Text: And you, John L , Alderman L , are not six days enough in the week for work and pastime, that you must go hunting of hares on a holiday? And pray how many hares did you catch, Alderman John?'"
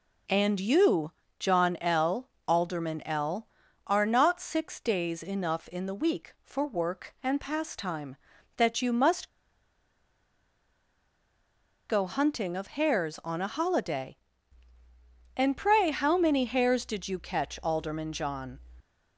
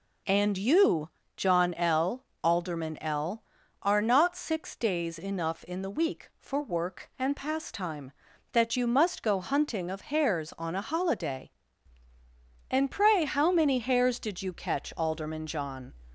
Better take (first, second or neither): second